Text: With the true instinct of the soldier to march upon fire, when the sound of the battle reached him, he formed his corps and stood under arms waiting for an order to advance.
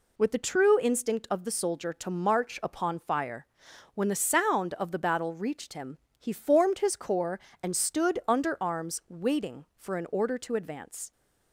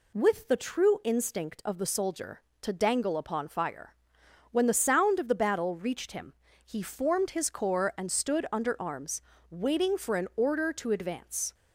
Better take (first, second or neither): first